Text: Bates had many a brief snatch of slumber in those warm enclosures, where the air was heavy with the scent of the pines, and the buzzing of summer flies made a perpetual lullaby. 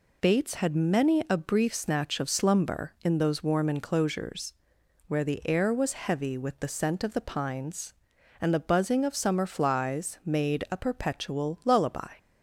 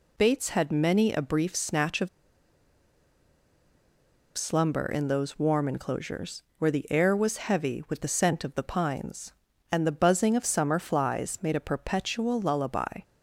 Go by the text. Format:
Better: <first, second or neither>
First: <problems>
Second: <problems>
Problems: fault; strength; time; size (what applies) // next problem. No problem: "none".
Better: first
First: none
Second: pauses between "of" and "slumber"; strong; at 2.0 s; 2.2 s long